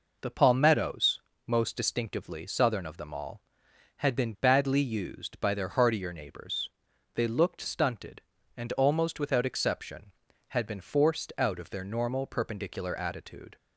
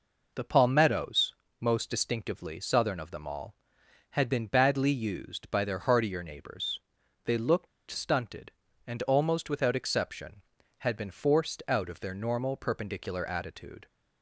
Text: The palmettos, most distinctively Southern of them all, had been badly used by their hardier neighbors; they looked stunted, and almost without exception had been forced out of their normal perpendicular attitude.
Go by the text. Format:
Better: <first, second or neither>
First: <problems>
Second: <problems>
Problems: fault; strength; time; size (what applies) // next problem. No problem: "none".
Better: first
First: none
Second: pauses between "looked" and "stunted"; slight; at 7.6 s; 0.22 s long